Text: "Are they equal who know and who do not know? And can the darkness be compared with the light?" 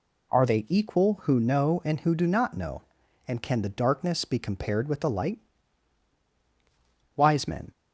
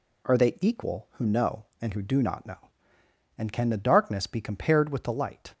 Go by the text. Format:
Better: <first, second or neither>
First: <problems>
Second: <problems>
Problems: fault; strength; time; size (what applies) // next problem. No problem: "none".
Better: second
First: goes on to say "Wise men"; from 7.1 s on; 0.56 s long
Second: none